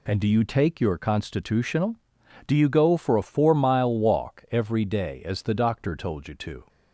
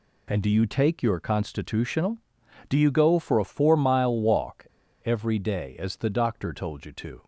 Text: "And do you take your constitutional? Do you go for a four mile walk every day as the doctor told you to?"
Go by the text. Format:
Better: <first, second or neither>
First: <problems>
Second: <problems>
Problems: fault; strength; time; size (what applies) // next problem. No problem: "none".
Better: first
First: none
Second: pauses between "walk" and "every"; at 4.6 s; 0.39 s long